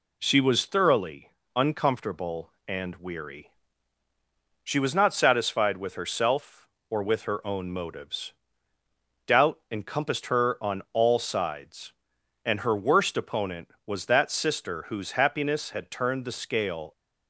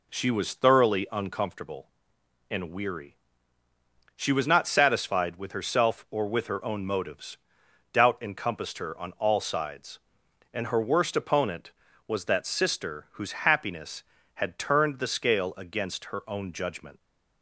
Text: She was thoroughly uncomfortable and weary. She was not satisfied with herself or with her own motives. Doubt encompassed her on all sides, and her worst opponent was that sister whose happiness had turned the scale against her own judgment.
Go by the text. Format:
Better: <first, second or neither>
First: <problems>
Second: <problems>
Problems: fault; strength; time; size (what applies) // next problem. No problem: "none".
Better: second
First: pauses between "thoroughly" and "uncomfortable"; slight; at 1.3 s; 0.24 s long // stops before "against her own judgment"; at 16.9 s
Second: none